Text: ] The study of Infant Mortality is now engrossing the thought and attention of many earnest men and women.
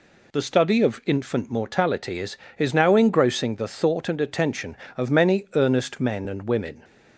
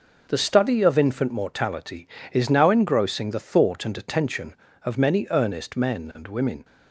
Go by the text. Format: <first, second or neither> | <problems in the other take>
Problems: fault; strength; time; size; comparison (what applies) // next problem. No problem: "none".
second | says "is" twice; at 2.5 s